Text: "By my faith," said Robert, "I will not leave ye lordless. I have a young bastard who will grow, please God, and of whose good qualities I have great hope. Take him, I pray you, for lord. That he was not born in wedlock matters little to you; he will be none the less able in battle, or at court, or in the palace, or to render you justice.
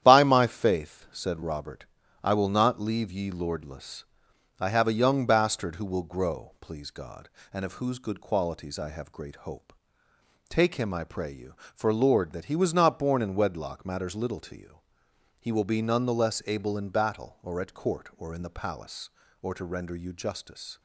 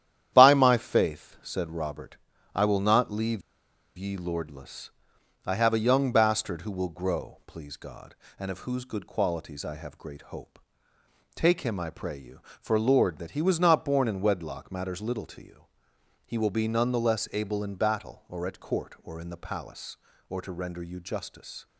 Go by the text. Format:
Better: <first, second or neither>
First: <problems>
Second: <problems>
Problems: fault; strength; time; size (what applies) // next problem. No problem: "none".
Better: first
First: starts louder than the rest; strong; until 1.0 s; 10.5 dB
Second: starts louder than the rest; strong; until 1.3 s; 10.5 dB // pauses between "leave" and "ye"; noticeable; at 3.4 s; 0.57 s long